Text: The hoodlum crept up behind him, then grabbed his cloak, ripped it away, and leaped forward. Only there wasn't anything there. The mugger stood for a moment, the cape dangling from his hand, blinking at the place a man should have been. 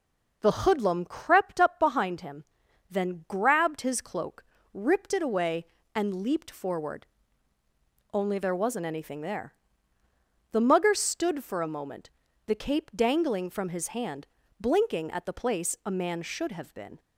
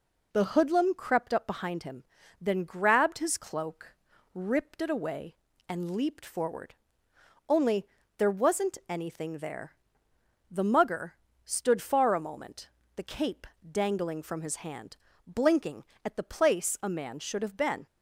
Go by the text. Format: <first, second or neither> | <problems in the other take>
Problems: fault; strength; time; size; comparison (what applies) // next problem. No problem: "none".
first | pauses between "Only" and "there"; slight; at 7.8 s; 0.32 s long // pauses between "mugger" and "stood"; slight; at 11.1 s; 0.32 s long // says "far" for "for"; at 11.8 s // pauses between "cape" and "dangling"; slight; at 13.4 s; 0.24 s long